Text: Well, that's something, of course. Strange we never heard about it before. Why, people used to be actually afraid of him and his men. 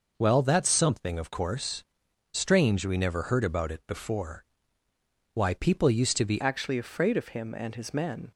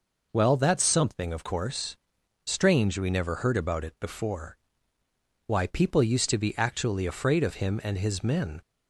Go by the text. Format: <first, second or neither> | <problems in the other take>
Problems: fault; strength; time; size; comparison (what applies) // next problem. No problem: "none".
second | changes voice at "actually"; from 6.4 s on; 1.9 s long